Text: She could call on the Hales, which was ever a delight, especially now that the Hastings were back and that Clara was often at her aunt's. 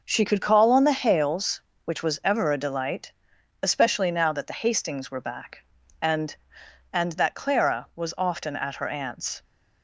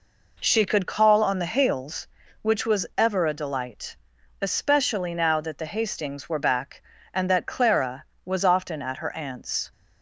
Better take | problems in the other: second | says "and" twice; at 6.9 s

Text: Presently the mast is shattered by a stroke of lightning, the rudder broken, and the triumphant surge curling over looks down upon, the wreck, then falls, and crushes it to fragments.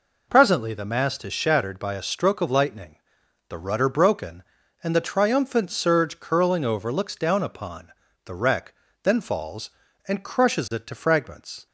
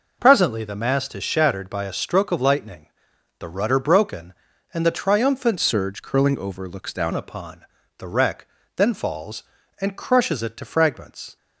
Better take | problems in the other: first | changes voice from "surge" to "down"; from 5.5 to 7.1 s; 1.6 s long

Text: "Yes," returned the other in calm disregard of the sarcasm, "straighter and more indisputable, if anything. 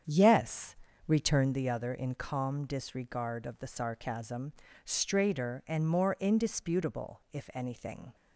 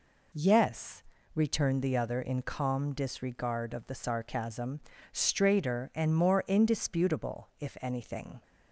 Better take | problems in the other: second | starts louder than the rest; strong; until 1.6 s; 8 dB

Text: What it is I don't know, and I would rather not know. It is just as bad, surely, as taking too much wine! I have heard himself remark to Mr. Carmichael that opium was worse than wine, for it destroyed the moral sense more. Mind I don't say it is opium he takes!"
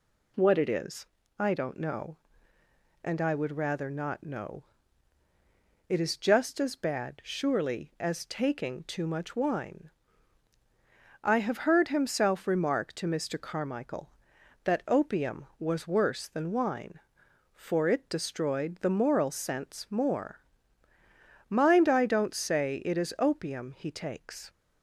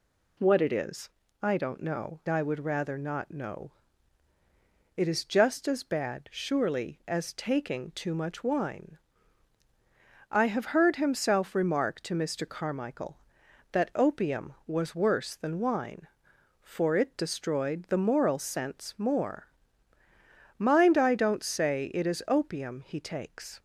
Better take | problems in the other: first | pauses between "is" and "I"; slight; at 1.0 s; 0.34 s long; slight in the first // skips "and"; at 2.2 s

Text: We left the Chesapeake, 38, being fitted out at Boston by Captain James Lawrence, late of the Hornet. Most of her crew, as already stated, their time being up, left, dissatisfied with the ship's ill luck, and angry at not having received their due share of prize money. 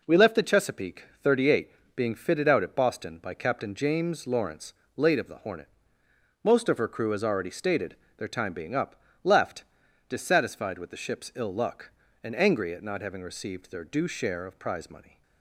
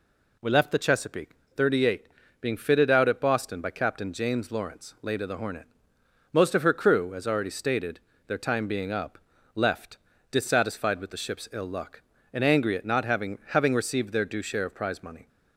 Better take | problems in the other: first | says "having" twice; at 13.4 s

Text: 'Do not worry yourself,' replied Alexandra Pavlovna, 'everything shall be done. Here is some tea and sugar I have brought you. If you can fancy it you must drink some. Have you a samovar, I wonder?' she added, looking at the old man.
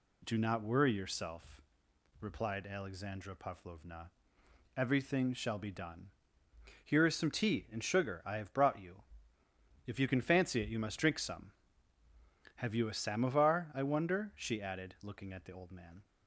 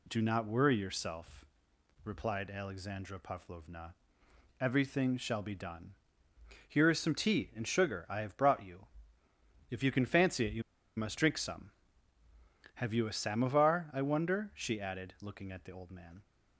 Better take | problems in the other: first | pauses between "you" and "must"; slight; at 10.6 s; 0.35 s long

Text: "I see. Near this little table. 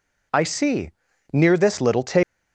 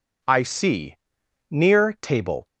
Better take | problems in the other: first | skips "this little"; at 1.9 s

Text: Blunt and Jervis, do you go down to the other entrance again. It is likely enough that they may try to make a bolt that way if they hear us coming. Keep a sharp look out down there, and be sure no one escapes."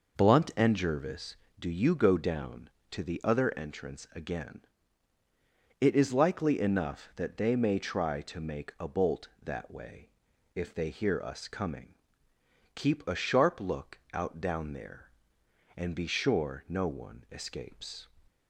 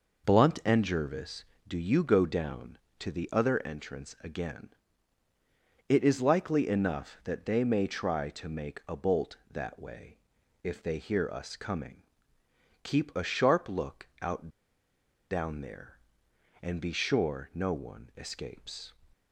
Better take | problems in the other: first | pauses between "way" and "if"; noticeable; at 10.1 s; 0.46 s long; noticeable in the first // pauses between "look" and "out"; slight; at 14.0 s; 0.16 s long; slight in the first // pauses between "out" and "down"; noticeable; at 14.4 s; 0.82 s long

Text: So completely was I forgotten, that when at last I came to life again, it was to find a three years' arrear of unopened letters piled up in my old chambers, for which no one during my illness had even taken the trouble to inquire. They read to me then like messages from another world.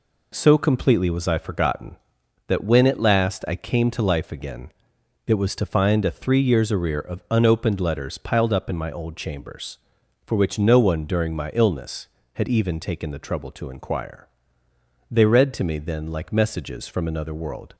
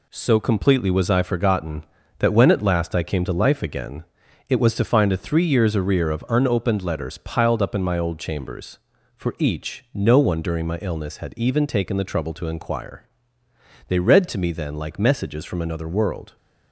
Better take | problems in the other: first | says "each" for "which"; at 9.3 s

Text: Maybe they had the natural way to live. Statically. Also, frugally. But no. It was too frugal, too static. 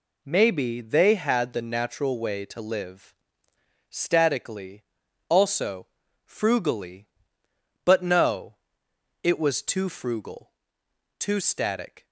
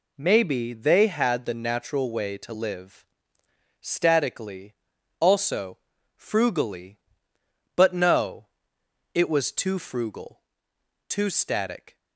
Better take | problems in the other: neither | none

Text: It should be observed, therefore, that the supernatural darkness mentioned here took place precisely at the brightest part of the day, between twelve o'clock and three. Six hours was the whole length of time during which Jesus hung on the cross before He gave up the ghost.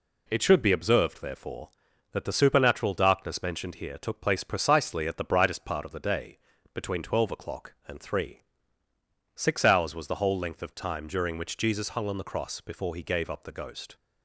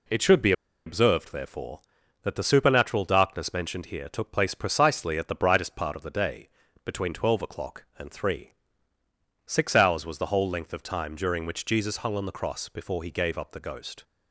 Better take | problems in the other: first | pauses between "be" and "observed"; slight; at 0.5 s; 0.34 s long

